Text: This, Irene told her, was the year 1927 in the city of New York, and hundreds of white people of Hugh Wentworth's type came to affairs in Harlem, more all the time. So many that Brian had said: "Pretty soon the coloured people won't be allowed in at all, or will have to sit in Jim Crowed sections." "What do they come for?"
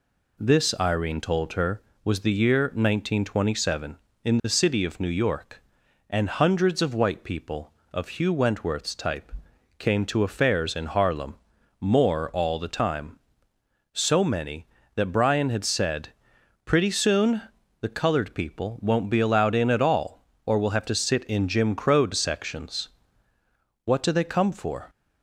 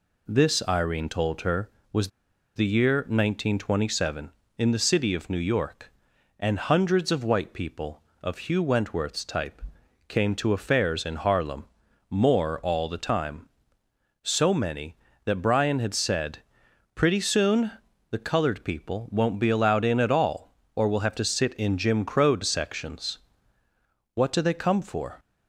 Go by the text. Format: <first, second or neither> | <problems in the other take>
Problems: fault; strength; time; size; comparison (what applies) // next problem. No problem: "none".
first | pauses between "was" and "the"; noticeable; at 2.0 s; 0.48 s long // pauses between "type" and "came"; noticeable; at 9.6 s; 0.46 s long; noticeable in the first // pauses between "soon" and "the"; at 17.7 s; 0.40 s long; also in the first